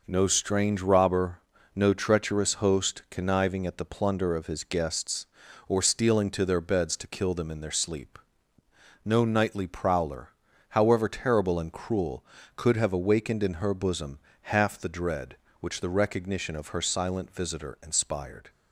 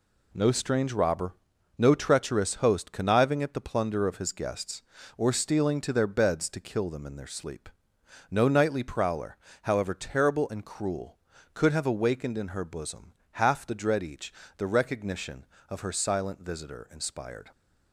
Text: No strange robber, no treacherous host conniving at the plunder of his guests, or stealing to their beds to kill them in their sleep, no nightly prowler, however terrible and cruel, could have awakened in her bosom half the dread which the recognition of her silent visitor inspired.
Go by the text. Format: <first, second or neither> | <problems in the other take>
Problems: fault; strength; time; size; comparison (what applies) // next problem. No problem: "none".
first | pauses between "bosom" and "half"; slight; at 13.1 s; 0.24 s long; slight in the first // says "each" for "which"; at 14.0 s